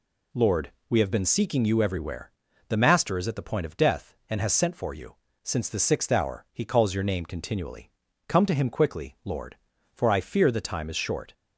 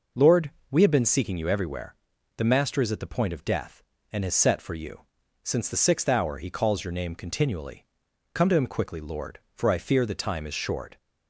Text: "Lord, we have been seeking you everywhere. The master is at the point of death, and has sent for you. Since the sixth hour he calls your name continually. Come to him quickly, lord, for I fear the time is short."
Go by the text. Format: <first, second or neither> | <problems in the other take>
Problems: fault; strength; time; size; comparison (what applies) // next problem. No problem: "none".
first | says "set" for "sent"; at 4.3 s